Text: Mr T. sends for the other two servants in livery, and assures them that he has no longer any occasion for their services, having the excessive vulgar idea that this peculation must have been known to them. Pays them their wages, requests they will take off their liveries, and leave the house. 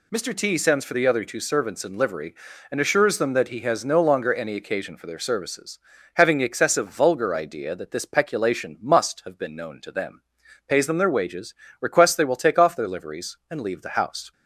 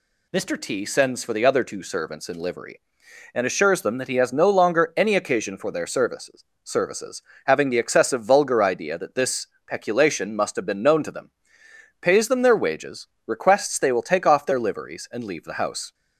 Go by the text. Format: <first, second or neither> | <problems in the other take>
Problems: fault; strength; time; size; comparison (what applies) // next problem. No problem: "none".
first | says "services" twice; at 6.6 s // pauses between "this" and "peculation"; slight; at 9.4 s; 0.20 s long